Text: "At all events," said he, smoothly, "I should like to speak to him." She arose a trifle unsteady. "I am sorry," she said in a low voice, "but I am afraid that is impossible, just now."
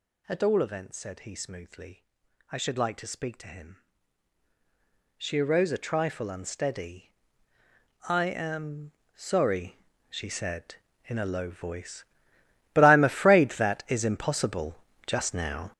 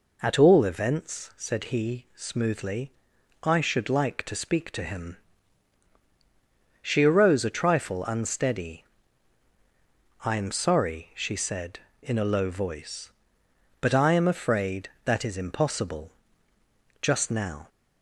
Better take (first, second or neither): second